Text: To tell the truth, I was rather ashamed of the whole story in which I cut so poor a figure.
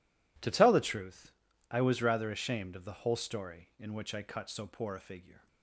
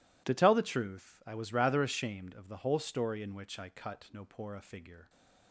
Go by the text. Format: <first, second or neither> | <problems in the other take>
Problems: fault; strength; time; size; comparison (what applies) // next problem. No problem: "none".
first | says "no" for "so"; at 4.1 s